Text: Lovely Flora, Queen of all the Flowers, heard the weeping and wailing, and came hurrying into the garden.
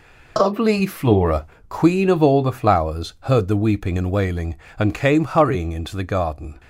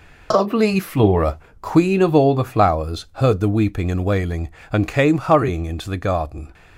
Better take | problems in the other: neither | none

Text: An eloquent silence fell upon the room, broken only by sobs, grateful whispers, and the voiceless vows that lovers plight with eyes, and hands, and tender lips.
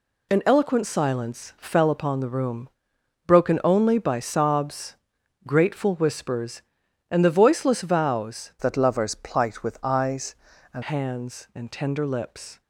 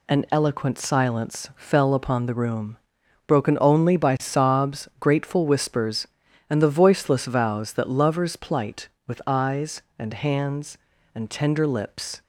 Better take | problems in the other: second | changes voice from "that" to "and"; from 8.5 to 10.8 s; 2.3 s long

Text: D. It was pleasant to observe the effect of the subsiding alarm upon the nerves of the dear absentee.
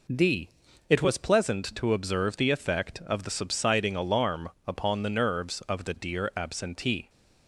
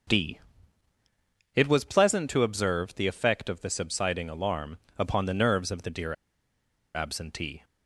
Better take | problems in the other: first | starts louder than the rest; until 2.2 s; 6.5 dB // pauses between "alarm" and "upon"; slight; at 4.7 s; 0.18 s long; slight in the first // pauses between "dear" and "absentee"; noticeable; at 6.1 s; 0.80 s long

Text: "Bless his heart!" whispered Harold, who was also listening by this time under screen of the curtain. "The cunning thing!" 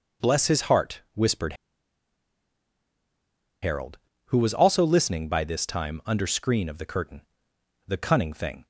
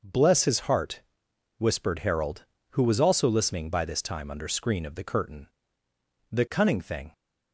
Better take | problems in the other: second | pauses between "whispered" and "Harold"; strong; at 1.5 s; 2.0 s long

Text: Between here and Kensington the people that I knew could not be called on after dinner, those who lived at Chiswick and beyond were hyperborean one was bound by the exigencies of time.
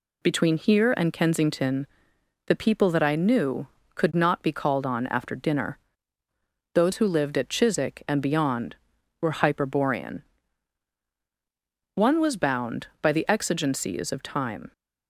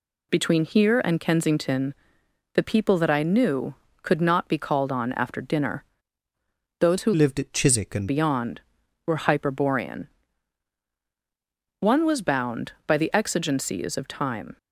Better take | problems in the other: first | pauses between "Kensington" and "the"; noticeable; at 1.9 s; 0.60 s long; noticeable in the first // changes voice from "lived" to "and"; from 7.1 to 8.0 s; 0.9 s long // pauses between "hyperborean" and "one"; strong; at 10.0 s; 1.7 s long; strong in the first

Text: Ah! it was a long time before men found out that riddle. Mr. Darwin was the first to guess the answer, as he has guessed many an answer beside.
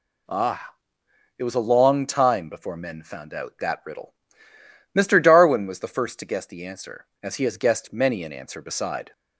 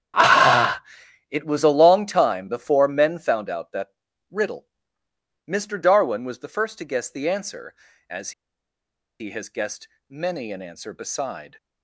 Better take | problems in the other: first | starts louder than the rest; strong; until 1.6 s; 10.5 dB // pauses between "that" and "riddle"; at 3.8 s; 0.42 s long // pauses between "as" and "he"; noticeable; at 8.3 s; 0.89 s long // pauses between "guessed" and "many"; slight; at 9.8 s; 0.22 s long

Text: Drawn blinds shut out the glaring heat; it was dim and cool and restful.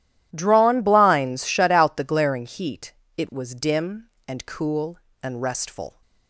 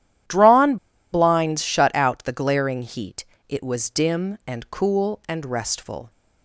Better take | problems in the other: first | pauses between "Drawn" and "blinds"; at 0.7 s; 0.36 s long

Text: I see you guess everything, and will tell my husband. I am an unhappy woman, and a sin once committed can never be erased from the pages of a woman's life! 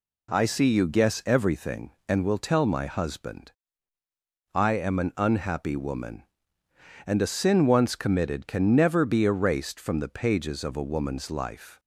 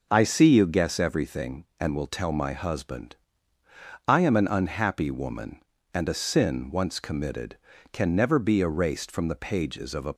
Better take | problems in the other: first | stops before "woman's life"; at 10.1 s

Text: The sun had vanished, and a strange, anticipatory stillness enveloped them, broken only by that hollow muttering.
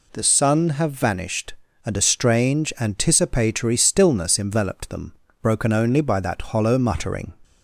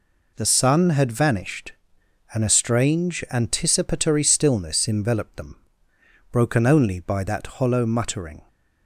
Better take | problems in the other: second | says "have" for "had"; at 0.6 s

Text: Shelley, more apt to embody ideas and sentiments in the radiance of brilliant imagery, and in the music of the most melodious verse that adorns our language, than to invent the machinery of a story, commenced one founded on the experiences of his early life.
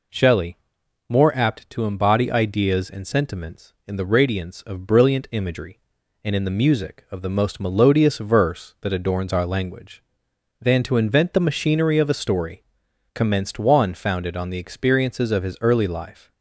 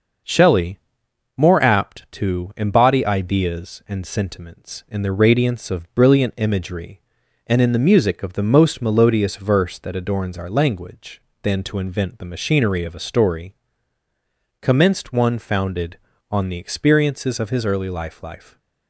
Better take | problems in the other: first | starts louder than the rest; until 1.8 s; 6.5 dB // says "life" twice; at 18.2 s

